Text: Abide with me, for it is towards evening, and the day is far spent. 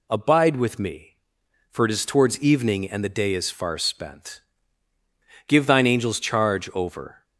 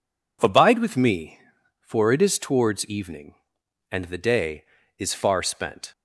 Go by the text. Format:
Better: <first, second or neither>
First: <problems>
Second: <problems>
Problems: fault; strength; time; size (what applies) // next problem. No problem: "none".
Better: second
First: goes on to say "Give thine angels charge over"; strong; from 5.4 s on; 1.7 s long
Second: none